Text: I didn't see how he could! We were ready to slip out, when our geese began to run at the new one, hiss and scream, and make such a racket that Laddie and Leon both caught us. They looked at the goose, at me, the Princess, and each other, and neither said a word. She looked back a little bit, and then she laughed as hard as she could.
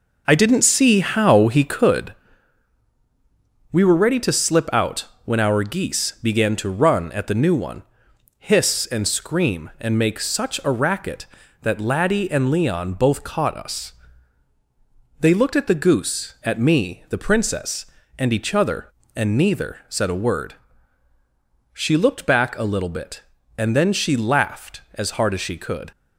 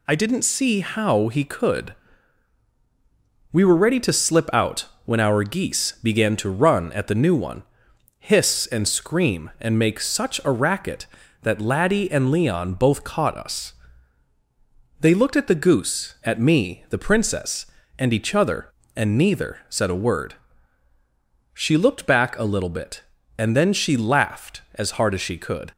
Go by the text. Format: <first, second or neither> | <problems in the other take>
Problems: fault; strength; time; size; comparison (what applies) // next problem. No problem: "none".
second | starts louder than the rest; noticeable; until 2.1 s; 5 dB